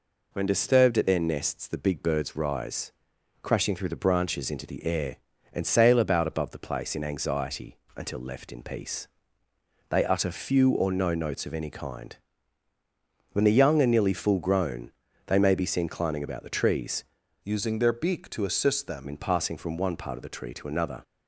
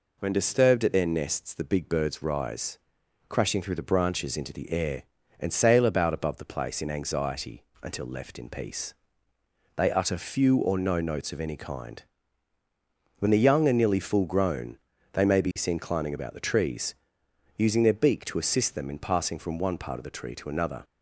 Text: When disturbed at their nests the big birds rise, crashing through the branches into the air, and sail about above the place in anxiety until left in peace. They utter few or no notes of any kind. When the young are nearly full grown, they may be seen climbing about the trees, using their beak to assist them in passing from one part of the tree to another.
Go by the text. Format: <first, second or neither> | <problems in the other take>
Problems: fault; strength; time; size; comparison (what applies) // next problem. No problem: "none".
second | pauses between "anxiety" and "until"; slight; at 7.7 s; 0.22 s long; slight in the second // changes voice from "using" to "them"; from 17.4 to 19.0 s; 1.6 s long